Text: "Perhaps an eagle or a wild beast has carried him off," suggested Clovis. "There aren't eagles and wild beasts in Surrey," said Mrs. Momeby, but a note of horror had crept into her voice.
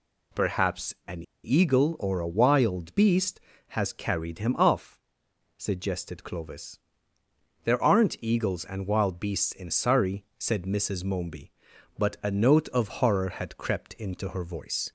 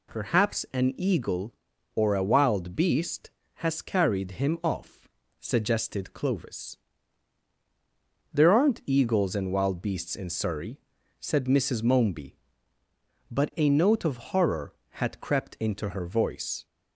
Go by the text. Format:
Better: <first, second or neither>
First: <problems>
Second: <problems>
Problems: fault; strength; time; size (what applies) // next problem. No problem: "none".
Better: second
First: pauses between "an" and "eagle"; slight; at 1.2 s; 0.21 s long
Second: none